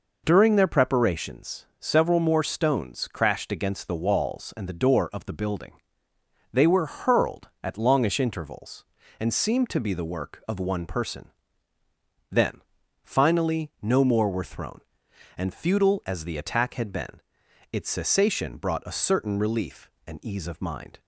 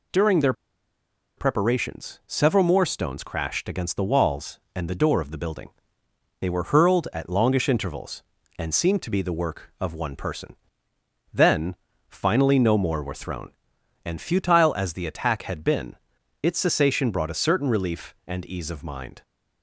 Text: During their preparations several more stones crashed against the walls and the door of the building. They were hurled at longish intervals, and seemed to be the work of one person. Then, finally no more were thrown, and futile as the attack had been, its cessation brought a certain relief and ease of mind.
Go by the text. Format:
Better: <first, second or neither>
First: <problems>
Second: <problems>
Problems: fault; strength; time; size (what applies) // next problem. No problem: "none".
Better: first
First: none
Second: pauses between "their" and "preparations"; noticeable; at 0.5 s; 0.85 s long